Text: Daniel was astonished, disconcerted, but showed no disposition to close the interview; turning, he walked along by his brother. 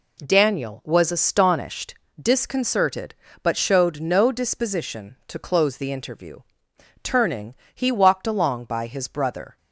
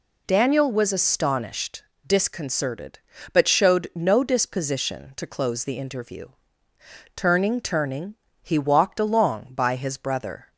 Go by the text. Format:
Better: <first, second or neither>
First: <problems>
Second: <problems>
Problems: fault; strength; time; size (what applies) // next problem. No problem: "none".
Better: first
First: none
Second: says "turning" twice; at 7.5 s